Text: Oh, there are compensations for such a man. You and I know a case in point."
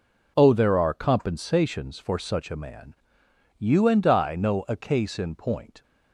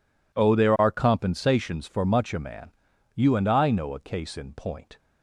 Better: first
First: none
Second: says "much" for "such"; at 2.0 s

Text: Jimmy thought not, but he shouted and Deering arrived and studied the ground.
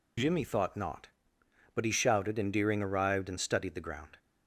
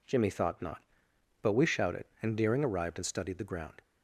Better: first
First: none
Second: says "we" for "he"; at 1.5 s

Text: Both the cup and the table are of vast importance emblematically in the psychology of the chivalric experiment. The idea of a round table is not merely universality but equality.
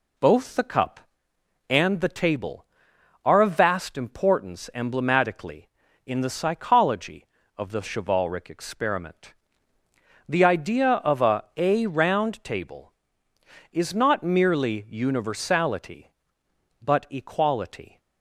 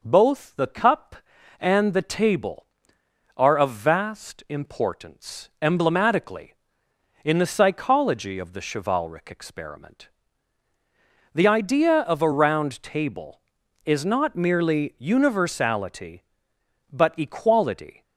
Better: second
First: says "a" twice; at 11.5 s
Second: none

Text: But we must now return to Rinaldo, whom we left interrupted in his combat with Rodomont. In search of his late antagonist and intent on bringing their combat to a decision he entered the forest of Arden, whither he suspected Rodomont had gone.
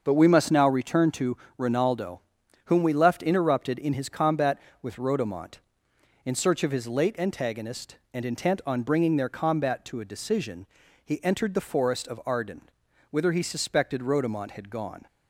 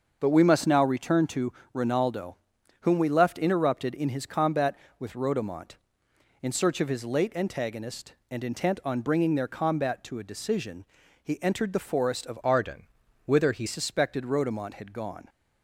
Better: first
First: starts louder than the rest; until 1.0 s; 6.5 dB // pauses between "to" and "Rinaldo"; slight; at 1.3 s; 0.22 s long // pauses between "decision" and "he"; at 10.6 s; 0.40 s long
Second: starts louder than the rest; until 1.2 s; 6.5 dB // pauses between "to" and "Rinaldo"; slight; at 1.5 s; 0.22 s long // pauses between "decision" and "he"; at 10.8 s; 0.40 s long // changes voice from "Arden" to "he"; from 12.4 to 13.6 s; 1.2 s long

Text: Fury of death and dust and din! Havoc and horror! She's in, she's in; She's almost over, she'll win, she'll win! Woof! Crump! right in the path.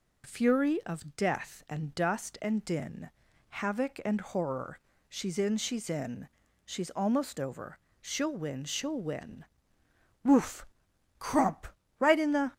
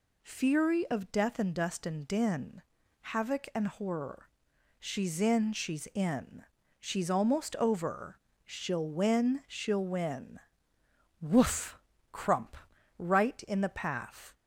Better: second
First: stops before "path"; at 12.5 s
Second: none

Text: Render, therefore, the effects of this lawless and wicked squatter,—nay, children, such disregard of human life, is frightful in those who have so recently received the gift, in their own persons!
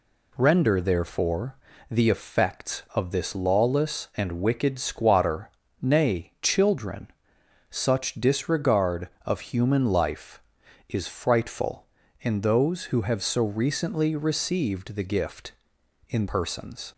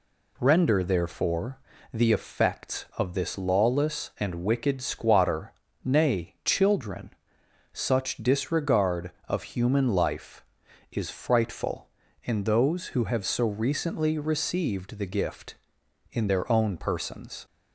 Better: second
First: skips "their own"; at 16.2 s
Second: none

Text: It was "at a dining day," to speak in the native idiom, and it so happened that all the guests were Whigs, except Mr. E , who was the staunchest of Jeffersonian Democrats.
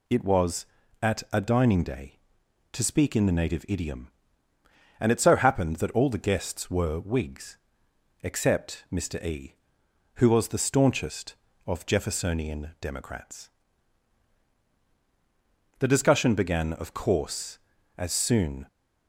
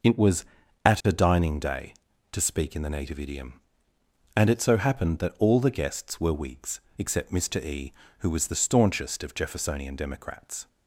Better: second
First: goes on to say "The discussion began of course as soon"; strong; from 15.7 s on; 2.8 s long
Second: none

